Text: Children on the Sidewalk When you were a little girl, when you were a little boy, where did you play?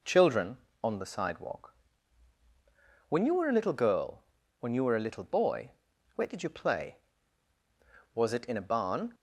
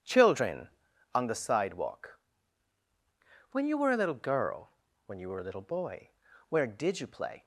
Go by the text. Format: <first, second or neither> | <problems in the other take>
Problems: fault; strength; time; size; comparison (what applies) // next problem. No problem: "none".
second | pauses between "Sidewalk" and "When"; strong; at 1.7 s; 1.3 s long; strong in the second // goes on to say "Was it in a barn"; noticeable; from 8.1 s on; 1.0 s long